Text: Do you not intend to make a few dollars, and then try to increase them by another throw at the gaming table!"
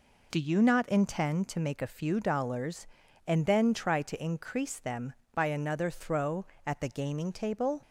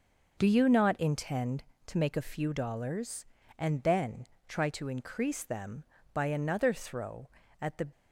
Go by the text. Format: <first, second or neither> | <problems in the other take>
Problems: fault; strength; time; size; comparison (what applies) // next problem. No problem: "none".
first | pauses between "then" and "try"; slight; at 4.2 s; 0.22 s long // stops before "gaming table"; at 7.9 s